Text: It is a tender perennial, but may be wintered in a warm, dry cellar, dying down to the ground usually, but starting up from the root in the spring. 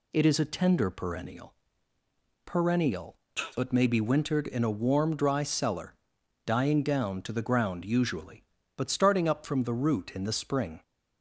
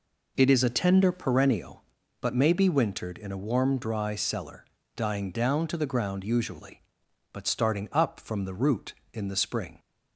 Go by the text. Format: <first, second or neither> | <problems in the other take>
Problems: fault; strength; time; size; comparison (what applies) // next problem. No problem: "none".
second | says "perennial" twice; at 2.4 s